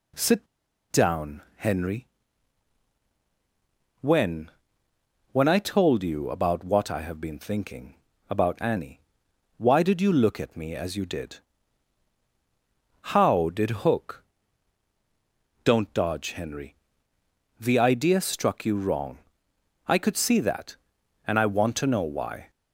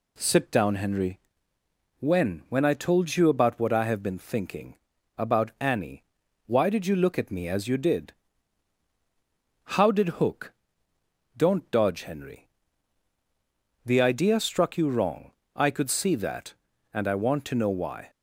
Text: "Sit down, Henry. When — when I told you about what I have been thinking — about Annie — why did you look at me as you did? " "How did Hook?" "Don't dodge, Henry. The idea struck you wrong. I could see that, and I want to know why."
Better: second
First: pauses between "Sit" and "down"; at 0.4 s; 0.45 s long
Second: none

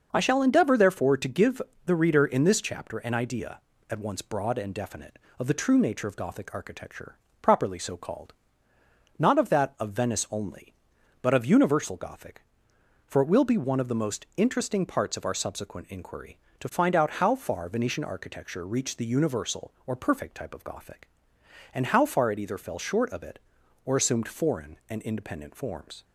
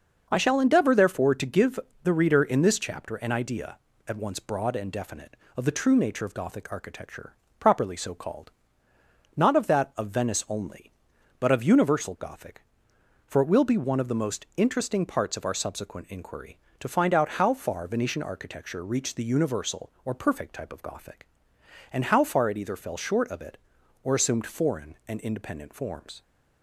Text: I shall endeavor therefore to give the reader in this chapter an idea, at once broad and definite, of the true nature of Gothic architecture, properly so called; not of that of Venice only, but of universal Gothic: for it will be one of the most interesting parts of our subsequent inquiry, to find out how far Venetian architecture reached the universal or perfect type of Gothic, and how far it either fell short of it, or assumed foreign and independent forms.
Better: neither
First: starts louder than the rest; noticeable; until 1.1 s; 6 dB // pauses between "give" and "the"; slight; at 1.6 s; 0.24 s long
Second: starts louder than the rest; until 1.3 s; 6 dB // pauses between "give" and "the"; slight; at 1.7 s; 0.24 s long

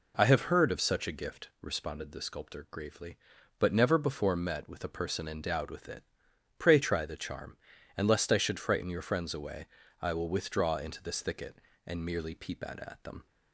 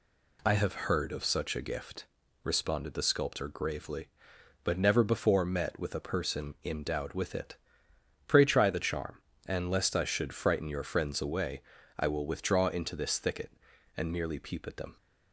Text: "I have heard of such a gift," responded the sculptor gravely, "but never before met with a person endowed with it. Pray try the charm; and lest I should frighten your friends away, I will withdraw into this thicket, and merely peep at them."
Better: second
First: says "at" twice; at 12.7 s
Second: none

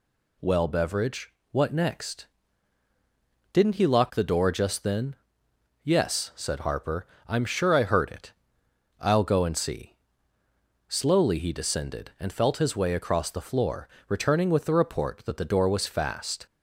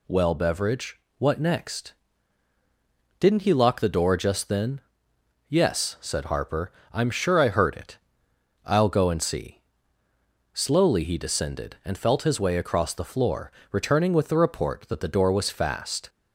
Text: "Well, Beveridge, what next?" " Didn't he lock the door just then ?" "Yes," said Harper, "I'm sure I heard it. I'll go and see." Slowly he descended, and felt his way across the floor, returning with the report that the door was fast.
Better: neither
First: none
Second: none

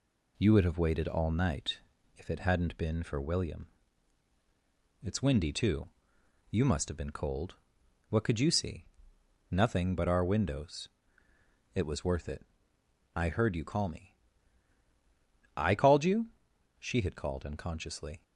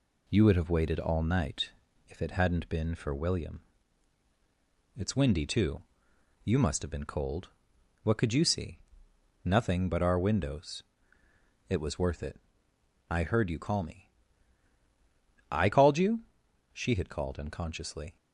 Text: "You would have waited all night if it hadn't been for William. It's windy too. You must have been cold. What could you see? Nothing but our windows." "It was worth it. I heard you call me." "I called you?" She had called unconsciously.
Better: neither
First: pauses between "night" and "if"; at 1.7 s; 0.38 s long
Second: pauses between "night" and "if"; at 1.7 s; 0.38 s long

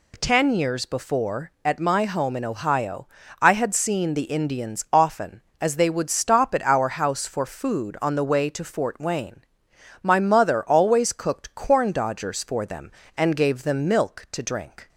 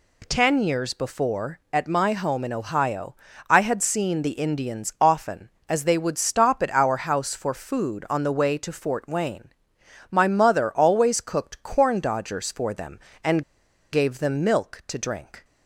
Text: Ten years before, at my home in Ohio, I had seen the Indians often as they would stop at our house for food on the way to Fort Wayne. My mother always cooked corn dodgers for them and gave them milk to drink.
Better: first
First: none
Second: pauses between "and" and "gave"; noticeable; at 13.4 s; 0.49 s long

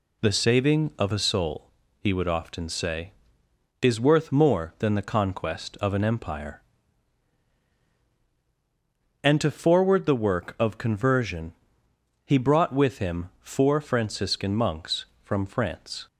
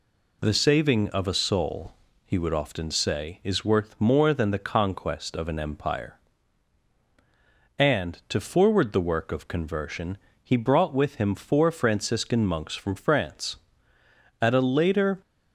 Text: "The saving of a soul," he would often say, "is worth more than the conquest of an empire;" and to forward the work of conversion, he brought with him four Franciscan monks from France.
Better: first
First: none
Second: goes on to say "At a later"; noticeable; from 14.4 s on; 0.80 s long

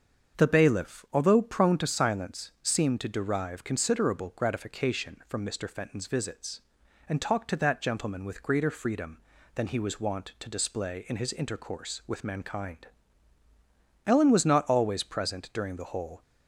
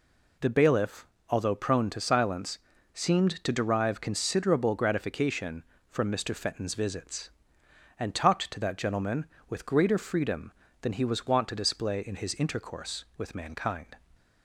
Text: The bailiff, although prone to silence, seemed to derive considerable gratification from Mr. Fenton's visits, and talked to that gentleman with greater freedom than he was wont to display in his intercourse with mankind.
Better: second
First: starts louder than the rest; until 1.4 s; 7 dB // goes on to say "Ellen was not always present during the whole"; strong; from 14.0 s on; 2.1 s long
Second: none

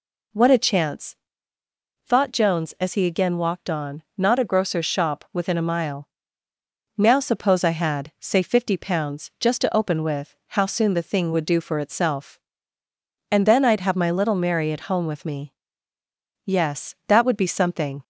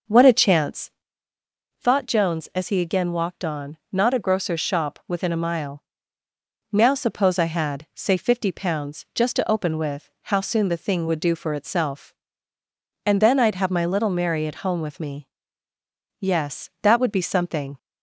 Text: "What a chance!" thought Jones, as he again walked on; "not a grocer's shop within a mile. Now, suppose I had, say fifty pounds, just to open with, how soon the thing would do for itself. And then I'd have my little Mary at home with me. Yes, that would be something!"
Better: first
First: none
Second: starts louder than the rest; noticeable; until 1.9 s; 6 dB

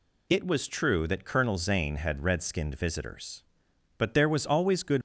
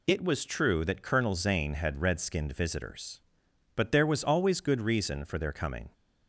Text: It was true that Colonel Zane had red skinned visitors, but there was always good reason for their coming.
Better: second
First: stops before "reason for their coming"; at 4.9 s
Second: none

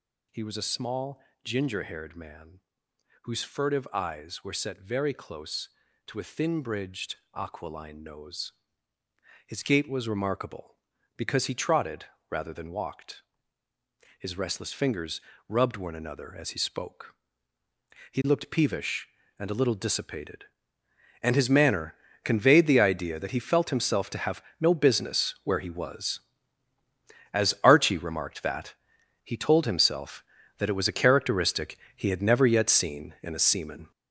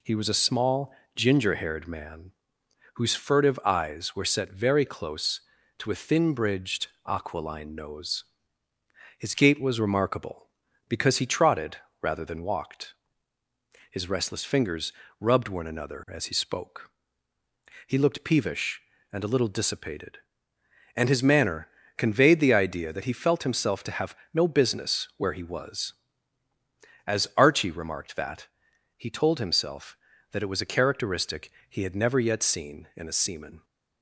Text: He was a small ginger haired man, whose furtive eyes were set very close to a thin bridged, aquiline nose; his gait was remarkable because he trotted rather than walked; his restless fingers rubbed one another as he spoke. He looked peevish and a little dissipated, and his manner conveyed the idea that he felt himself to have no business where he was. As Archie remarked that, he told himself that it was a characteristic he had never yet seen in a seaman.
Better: second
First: gets louder; strong; throughout; 8 dB // pauses between "small" and "ginger"; slight; at 1.2 s; 0.22 s long // pauses between "trotted" and "rather"; slight; at 12.0 s; 0.24 s long // pauses between "fingers" and "rubbed"; slight; at 15.2 s; 0.28 s long // pauses between "manner" and "conveyed"; slight; at 21.9 s; 0.28 s long // pauses between "have" and "no"; slight; at 24.4 s; 0.18 s long // pauses between "characteristic" and "he"; slight; at 31.7 s; 0.16 s long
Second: pauses between "small" and "ginger"; slight; at 0.9 s; 0.22 s long // pauses between "trotted" and "rather"; slight; at 11.7 s; 0.24 s long // pauses between "fingers" and "rubbed"; slight; at 14.9 s; 0.28 s long // pauses between "manner" and "conveyed"; slight; at 21.6 s; 0.28 s long // pauses between "have" and "no"; slight; at 24.1 s; 0.18 s long // pauses between "characteristic" and "he"; slight; at 31.5 s; 0.16 s long

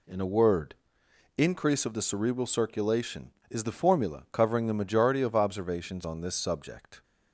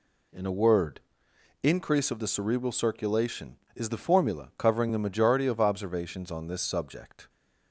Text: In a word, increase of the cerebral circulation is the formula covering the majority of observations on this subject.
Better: neither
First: none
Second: none

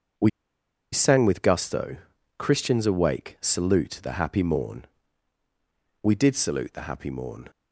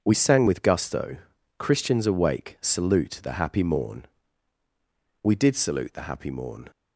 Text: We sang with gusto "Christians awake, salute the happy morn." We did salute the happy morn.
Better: second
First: pauses between "We" and "sang"; noticeable; at 0.2 s; 0.62 s long // pauses between "gusto" and "Christians"; at 1.9 s; 0.42 s long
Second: pauses between "gusto" and "Christians"; at 1.1 s; 0.42 s long

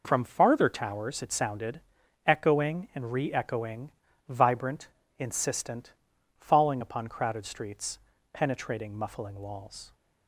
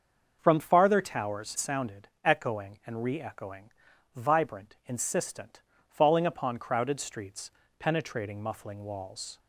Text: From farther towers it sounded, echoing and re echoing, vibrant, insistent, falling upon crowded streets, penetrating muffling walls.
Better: first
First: none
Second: starts louder than the rest; until 1.4 s; 6.5 dB // skips "it"; at 1.5 s

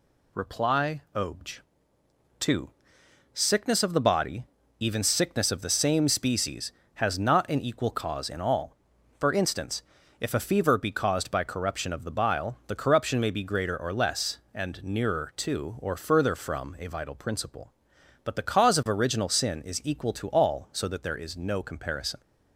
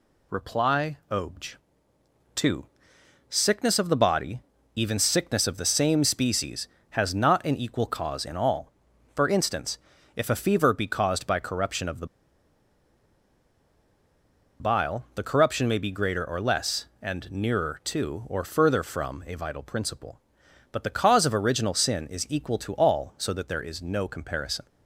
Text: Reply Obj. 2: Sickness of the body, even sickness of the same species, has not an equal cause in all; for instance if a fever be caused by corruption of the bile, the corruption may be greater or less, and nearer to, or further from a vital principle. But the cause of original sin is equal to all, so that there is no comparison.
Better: first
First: pauses between "instance" and "if"; slight; at 9.8 s; 0.36 s long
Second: pauses between "instance" and "if"; slight; at 9.7 s; 0.36 s long // pauses between "the" and "bile"; strong; at 12.0 s; 2.5 s long

